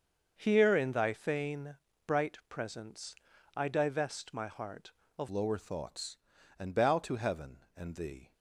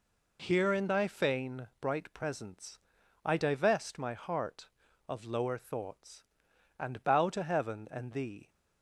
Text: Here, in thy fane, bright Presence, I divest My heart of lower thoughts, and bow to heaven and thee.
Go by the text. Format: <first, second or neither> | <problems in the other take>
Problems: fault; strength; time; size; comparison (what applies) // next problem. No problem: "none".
second | starts louder than the rest; until 1.3 s; 6.5 dB // changes voice at "lower"; from 5.3 s on; 3.0 s long